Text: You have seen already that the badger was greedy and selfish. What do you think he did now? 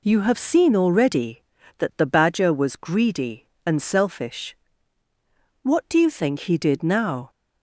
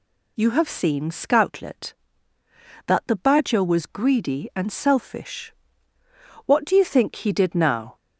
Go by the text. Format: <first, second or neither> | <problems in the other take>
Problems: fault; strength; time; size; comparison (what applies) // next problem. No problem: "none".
first | says "scoutlet" for "already"; at 1.1 s